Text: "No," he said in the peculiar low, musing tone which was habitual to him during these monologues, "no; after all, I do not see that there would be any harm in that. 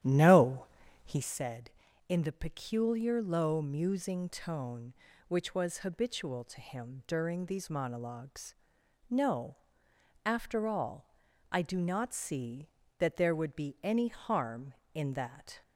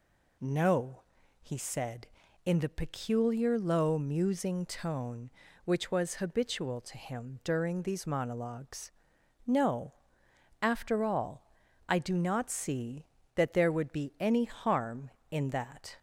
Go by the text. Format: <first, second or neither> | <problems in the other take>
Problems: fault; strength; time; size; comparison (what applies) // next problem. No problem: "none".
second | starts louder than the rest; strong; until 1.4 s; 11 dB